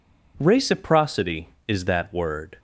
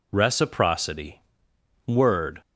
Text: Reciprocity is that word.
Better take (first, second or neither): first